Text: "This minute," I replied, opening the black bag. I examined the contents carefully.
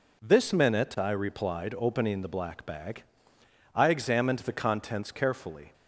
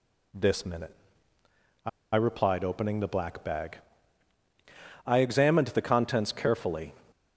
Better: first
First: none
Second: pauses between "I" and "replied"; slight; at 1.8 s; 0.25 s long

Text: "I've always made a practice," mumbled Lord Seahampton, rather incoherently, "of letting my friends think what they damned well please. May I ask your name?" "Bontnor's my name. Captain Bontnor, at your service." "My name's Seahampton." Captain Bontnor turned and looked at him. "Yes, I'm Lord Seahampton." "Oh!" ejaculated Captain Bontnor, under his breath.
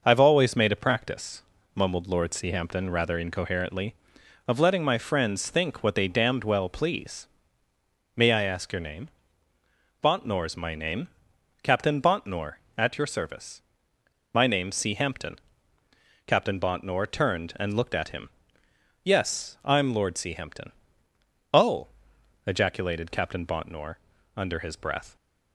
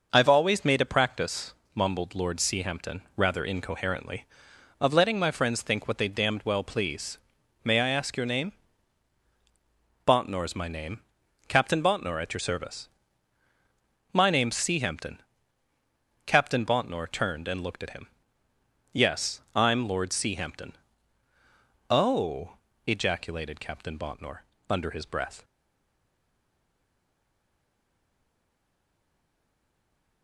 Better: first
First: none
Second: stays silent after the last word; strong; from 25.4 s on; 4.8 s long

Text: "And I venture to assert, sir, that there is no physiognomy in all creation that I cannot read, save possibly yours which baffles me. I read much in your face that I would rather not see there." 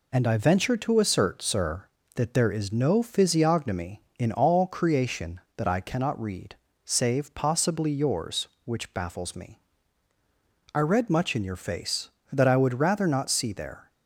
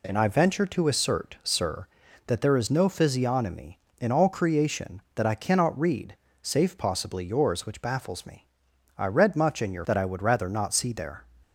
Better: first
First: none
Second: skips "face"; at 9.8 s

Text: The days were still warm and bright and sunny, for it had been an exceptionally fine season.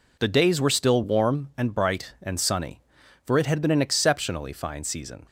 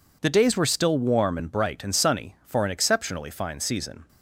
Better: first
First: none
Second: skips "it had been"; at 2.6 s

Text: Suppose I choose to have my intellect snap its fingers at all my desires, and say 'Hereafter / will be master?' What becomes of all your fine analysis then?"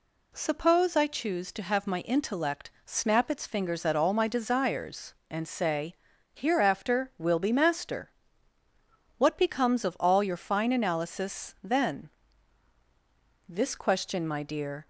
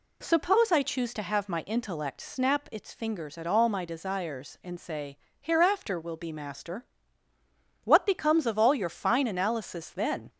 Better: second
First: pauses between "say" and "Hereafter"; at 5.9 s; 0.40 s long // goes on to say "This question my dear"; from 13.4 s on; 1.4 s long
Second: pauses between "say" and "Hereafter"; slight; at 5.1 s; 0.22 s long

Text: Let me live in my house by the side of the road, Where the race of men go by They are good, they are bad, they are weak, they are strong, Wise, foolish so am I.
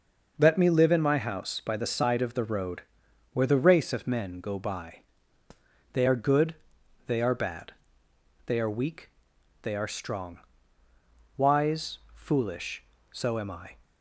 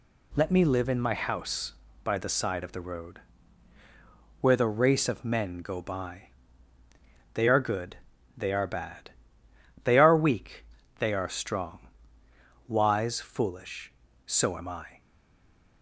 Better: first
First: pauses between "by" and "They"; noticeable; at 5.0 s; 0.92 s long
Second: pauses between "by" and "They"; at 6.2 s; 1.0 s long // stays silent after the last word; slight; from 15.0 s on; 0.8 s long

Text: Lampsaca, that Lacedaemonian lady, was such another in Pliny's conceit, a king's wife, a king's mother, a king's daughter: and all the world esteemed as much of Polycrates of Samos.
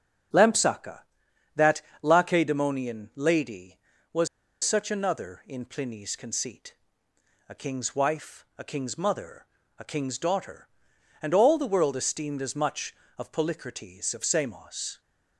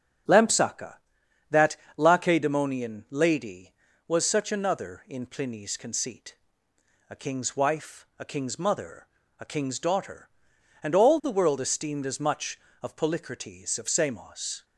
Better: second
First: starts louder than the rest; strong; until 2.1 s; 7.5 dB // pauses between "that" and "Lacedaemonian"; slight; at 1.8 s; 0.22 s long // pauses between "was" and "such"; at 4.2 s; 0.36 s long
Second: starts louder than the rest; strong; until 2.0 s; 7.5 dB // pauses between "that" and "Lacedaemonian"; slight; at 1.7 s; 0.22 s long

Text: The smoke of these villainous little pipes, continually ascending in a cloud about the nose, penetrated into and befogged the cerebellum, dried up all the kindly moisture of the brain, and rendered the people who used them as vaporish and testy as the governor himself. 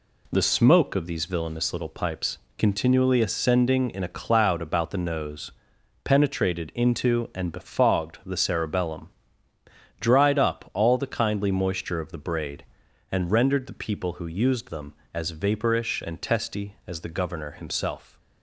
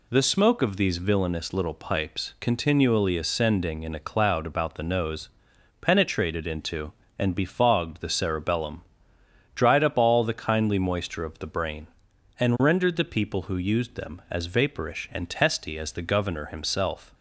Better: second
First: says "braid" for "brain"; at 12.2 s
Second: none

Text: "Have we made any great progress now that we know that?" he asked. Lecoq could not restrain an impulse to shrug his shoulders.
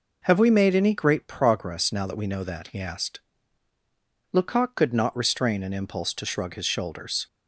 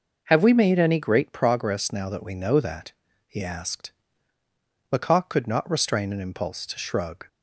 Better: first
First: none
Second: stops before "his shoulders"; at 7.2 s

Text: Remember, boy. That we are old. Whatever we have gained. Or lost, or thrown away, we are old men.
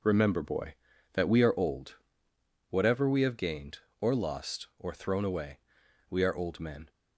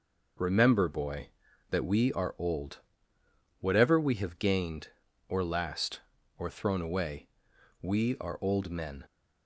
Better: first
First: none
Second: says "last" for "lost"; at 5.4 s

